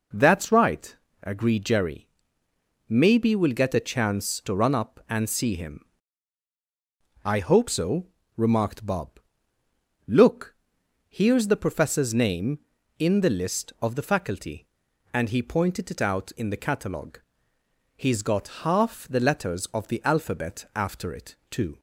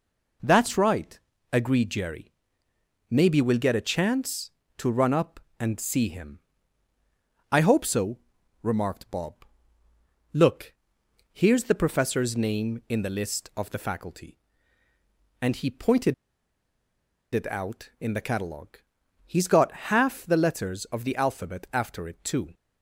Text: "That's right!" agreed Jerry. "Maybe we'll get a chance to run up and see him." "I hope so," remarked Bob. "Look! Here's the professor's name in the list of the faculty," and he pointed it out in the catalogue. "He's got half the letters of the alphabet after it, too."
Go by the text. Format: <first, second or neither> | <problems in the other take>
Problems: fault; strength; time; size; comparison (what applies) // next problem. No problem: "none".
first | pauses between "pointed" and "it"; at 16.1 s; 1.1 s long